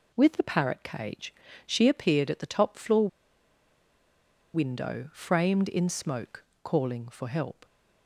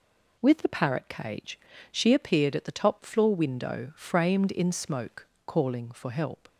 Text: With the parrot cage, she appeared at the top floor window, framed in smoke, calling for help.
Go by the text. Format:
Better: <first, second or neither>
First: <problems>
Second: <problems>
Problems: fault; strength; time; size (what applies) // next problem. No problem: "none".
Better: second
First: pauses between "floor" and "window"; strong; at 3.0 s; 1.4 s long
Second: none